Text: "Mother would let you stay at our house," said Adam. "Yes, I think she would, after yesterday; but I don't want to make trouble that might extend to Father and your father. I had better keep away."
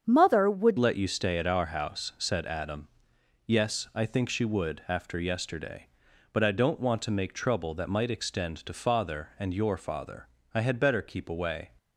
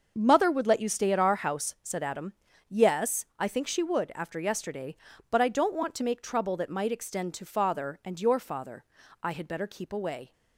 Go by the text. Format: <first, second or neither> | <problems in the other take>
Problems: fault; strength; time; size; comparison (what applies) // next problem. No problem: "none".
second | starts louder than the rest; strong; until 1.0 s; 7.5 dB; also in the second // changes voice at "let"; from 0.7 s on; 10.9 s long